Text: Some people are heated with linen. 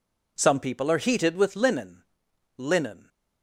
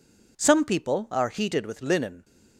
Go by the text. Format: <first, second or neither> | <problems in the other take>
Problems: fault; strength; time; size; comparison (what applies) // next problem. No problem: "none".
second | says "linen" twice; at 2.5 s